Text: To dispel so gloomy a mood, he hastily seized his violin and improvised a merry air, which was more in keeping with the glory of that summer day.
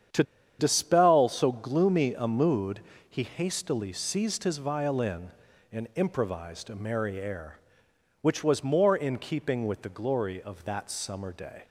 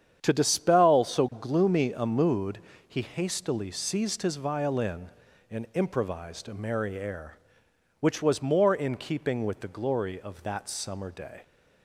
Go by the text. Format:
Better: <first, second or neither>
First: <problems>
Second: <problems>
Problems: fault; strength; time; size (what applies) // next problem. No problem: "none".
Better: second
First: starts louder than the rest; strong; until 1.4 s; 8.5 dB // pauses between "To" and "dispel"; at 0.2 s; 0.36 s long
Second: starts louder than the rest; strong; until 1.2 s; 8.5 dB